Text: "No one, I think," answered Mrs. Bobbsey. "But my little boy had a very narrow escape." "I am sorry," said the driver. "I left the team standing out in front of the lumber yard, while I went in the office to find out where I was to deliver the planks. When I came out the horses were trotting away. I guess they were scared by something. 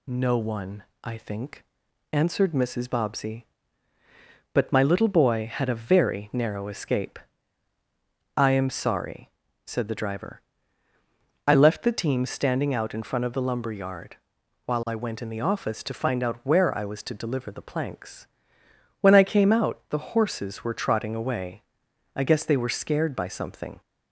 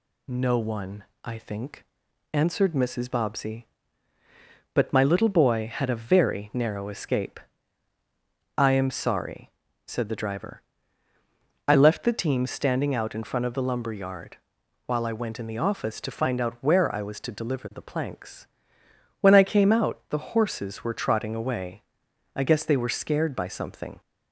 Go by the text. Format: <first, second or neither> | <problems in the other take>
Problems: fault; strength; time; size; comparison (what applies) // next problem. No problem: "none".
neither | none